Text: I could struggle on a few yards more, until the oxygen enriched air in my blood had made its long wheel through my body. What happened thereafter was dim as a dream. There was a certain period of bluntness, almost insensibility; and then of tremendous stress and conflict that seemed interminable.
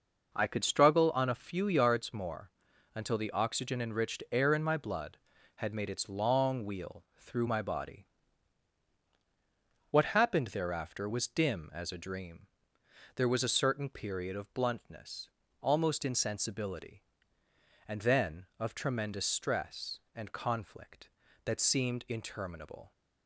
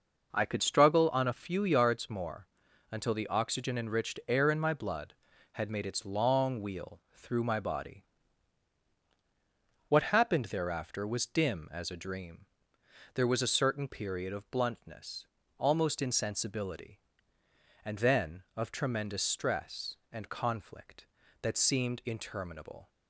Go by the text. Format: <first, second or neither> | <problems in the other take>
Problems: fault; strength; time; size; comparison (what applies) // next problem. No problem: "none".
neither | none